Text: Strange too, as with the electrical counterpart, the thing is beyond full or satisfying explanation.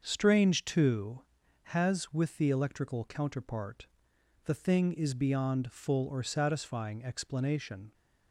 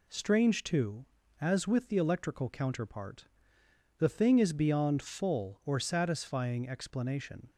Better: second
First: starts louder than the rest; until 1.0 s; 6.5 dB // says "has" for "as"; at 1.6 s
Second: none

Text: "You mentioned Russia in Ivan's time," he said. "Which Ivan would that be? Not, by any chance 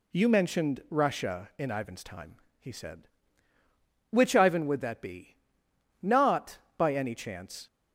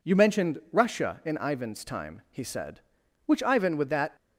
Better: first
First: none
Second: stops before "be Not by any chance"; at 4.1 s

